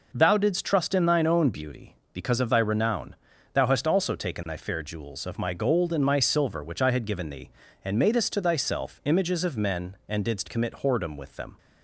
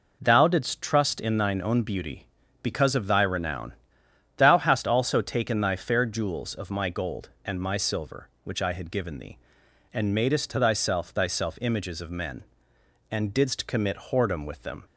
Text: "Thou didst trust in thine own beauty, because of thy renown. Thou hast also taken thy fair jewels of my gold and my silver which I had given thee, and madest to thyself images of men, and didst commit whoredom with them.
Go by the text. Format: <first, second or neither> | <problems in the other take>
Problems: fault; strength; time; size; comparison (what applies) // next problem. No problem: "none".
first | says "thyself" twice; at 11.0 s